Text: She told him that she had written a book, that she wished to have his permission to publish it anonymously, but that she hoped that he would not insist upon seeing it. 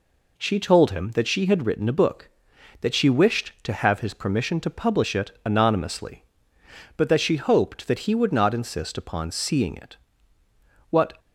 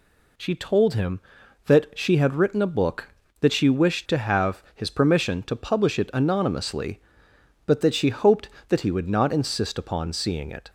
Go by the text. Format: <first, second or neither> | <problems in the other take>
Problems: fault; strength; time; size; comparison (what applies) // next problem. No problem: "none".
second | goes on to say "What"; slight; from 10.9 s on; 0.28 s long